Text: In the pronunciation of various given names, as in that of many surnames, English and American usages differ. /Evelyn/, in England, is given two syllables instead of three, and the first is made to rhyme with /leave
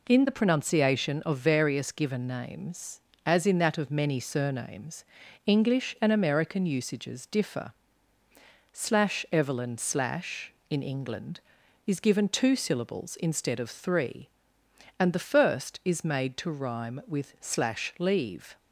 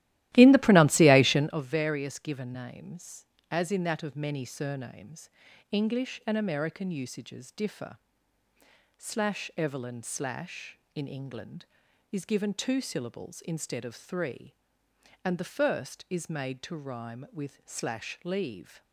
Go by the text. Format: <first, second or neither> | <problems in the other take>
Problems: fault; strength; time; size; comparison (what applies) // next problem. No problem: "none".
first | starts louder than the rest; strong; until 1.6 s; 15.5 dB